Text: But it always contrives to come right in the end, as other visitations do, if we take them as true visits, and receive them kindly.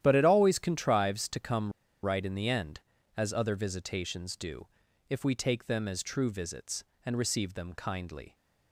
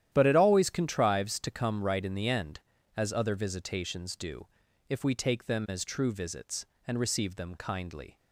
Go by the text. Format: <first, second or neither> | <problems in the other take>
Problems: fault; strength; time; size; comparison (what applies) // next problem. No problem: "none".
second | starts louder than the rest; strong; until 1.0 s; 11.5 dB; strong in the second // pauses between "come" and "right"; slight; at 1.7 s; 0.31 s long